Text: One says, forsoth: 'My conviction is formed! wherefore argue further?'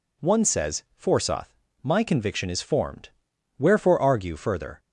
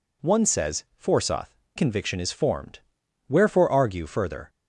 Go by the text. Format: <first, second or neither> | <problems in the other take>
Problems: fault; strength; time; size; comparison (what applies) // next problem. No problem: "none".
first | skips "My"; at 1.6 s